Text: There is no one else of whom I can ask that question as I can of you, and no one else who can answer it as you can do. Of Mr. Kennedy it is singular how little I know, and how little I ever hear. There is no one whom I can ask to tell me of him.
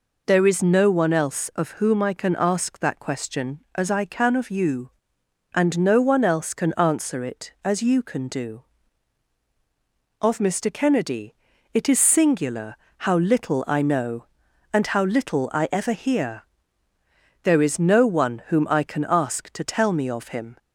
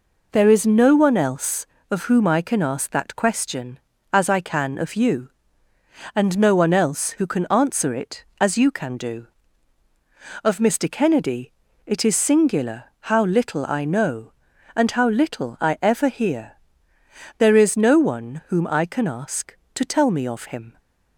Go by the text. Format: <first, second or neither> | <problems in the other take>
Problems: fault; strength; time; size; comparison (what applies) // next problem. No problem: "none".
second | skips "who"; at 6.5 s // pauses between "Kennedy" and "it"; at 11.3 s; 0.40 s long; slight in the second // pauses between "singular" and "how"; slight; at 12.7 s; 0.24 s long; slight in the second